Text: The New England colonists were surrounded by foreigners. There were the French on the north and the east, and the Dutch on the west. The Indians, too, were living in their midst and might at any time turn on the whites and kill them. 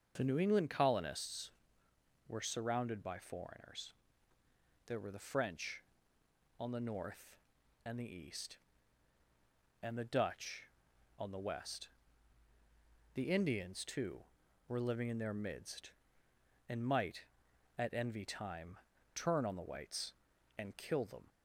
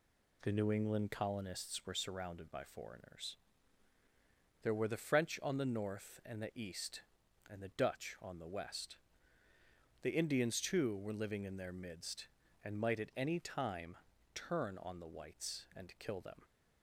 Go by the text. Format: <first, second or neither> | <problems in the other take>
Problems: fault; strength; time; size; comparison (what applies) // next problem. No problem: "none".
second | starts louder than the rest; until 1.1 s; 6.5 dB // says "envy" for "any"; at 17.9 s // pauses between "time" and "turn"; slight; at 18.7 s; 0.36 s long; slight in the second